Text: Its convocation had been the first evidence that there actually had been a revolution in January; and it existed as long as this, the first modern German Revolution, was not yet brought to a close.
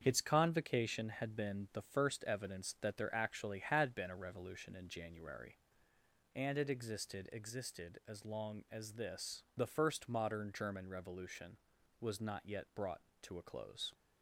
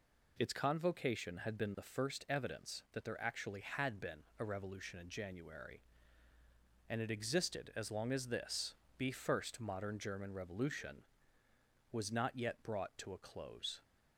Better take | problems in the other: second | starts louder than the rest; strong; until 1.0 s; 7.5 dB // says "existed" twice; at 7.3 s

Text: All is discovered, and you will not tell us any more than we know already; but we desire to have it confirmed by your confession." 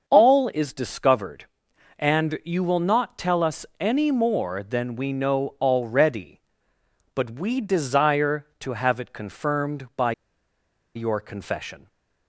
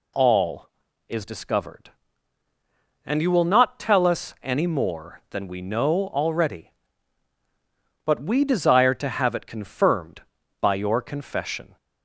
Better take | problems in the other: second | starts louder than the rest; until 1.1 s; 6.5 dB // pauses between "by" and "your"; noticeable; at 10.1 s; 0.82 s long

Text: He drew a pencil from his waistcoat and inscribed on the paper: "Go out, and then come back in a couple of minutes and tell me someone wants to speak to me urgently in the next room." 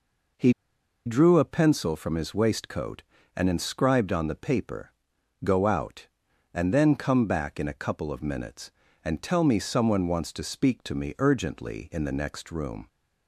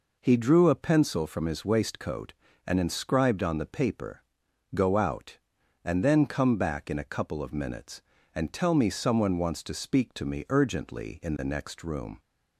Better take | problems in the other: second | pauses between "He" and "drew"; noticeable; at 0.5 s; 0.53 s long

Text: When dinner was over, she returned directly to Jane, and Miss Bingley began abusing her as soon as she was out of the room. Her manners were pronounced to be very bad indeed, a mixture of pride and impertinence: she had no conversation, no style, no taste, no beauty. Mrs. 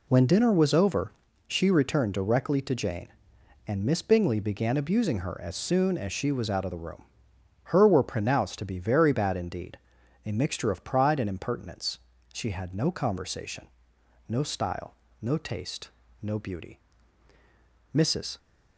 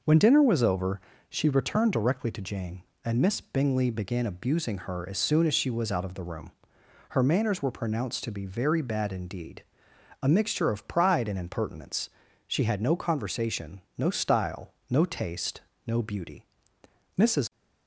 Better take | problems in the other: second | skips "manners"; at 7.8 s

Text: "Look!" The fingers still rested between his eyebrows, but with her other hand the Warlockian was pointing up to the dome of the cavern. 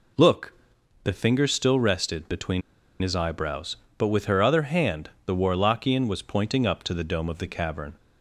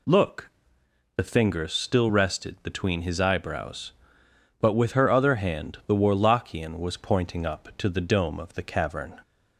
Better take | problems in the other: second | pauses between "between" and "his"; at 2.6 s; 0.40 s long // pauses between "hand" and "the"; slight; at 5.0 s; 0.16 s long

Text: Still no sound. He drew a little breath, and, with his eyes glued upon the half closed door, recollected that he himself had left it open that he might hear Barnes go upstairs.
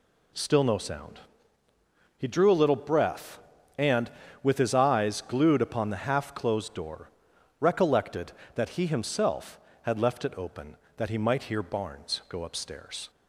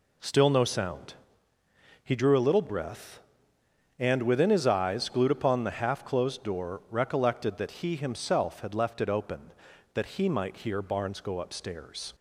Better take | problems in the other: first | says "within" for "with"; at 4.2 s

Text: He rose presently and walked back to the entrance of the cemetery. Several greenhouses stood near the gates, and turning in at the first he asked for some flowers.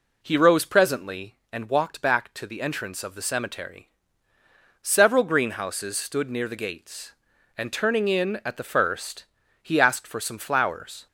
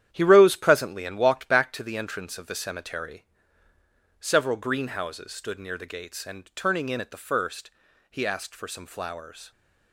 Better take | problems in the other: first | gets quieter; strong; throughout; 8.5 dB // pauses between "first" and "he"; at 7.6 s; 0.40 s long; also in the first

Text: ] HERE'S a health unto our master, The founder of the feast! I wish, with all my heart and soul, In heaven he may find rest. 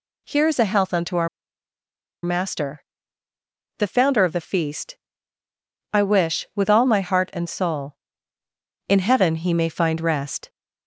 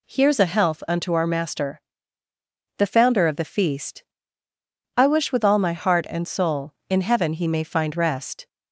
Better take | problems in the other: second | pauses between "our" and "master"; noticeable; at 1.2 s; 0.95 s long

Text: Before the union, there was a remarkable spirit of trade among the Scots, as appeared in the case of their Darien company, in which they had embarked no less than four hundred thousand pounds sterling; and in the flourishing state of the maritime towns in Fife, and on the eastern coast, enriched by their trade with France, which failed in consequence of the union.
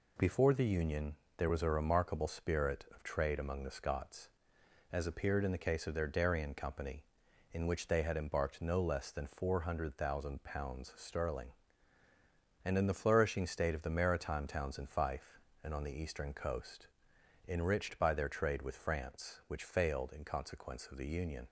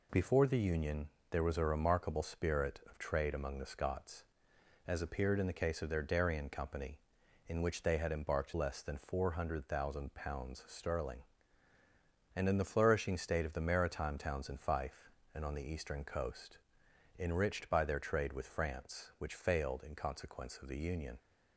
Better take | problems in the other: first | skips "no"; at 8.5 s

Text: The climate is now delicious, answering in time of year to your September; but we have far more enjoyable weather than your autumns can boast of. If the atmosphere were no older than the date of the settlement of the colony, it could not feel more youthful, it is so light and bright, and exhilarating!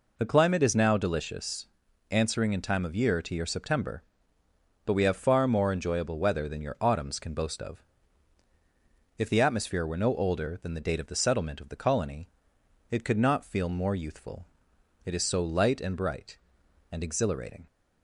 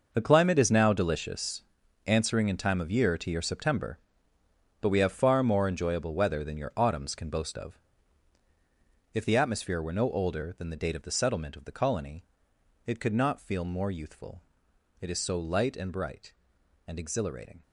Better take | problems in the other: first | gets quieter; strong; throughout; 12.5 dB

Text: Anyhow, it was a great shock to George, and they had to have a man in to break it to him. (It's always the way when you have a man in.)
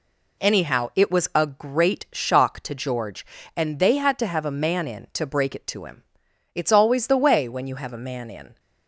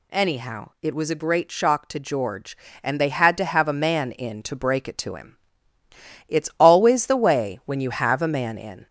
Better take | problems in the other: first | gets louder; slight; throughout; 2 dB

